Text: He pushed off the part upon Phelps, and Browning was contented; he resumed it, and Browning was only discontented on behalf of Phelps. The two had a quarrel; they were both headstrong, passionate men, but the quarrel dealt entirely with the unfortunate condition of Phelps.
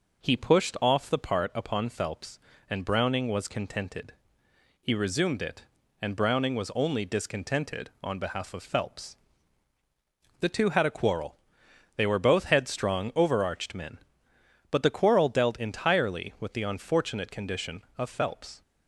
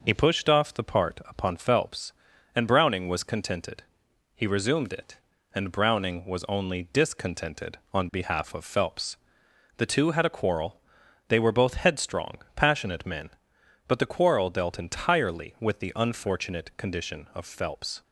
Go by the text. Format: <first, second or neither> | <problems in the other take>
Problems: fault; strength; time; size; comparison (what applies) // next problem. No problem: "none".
second | says "overarched" for "passionate"; at 13.1 s